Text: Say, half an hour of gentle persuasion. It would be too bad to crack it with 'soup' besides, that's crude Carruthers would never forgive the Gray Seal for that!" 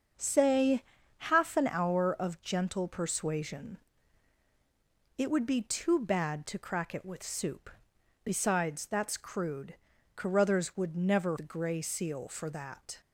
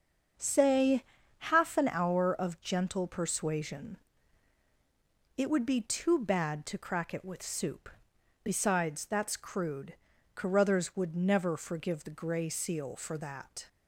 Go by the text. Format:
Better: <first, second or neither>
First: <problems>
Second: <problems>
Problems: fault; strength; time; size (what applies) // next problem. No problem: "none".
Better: second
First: starts louder than the rest; until 1.5 s; 6.5 dB // pauses between "soup" and "besides"; noticeable; at 7.7 s; 0.52 s long // pauses between "crude" and "Carruthers"; at 9.7 s; 0.40 s long // skips "forgive"; at 11.3 s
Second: starts louder than the rest; until 1.7 s; 6.5 dB // pauses between "soup" and "besides"; noticeable; at 7.8 s; 0.52 s long // pauses between "crude" and "Carruthers"; at 9.9 s; 0.40 s long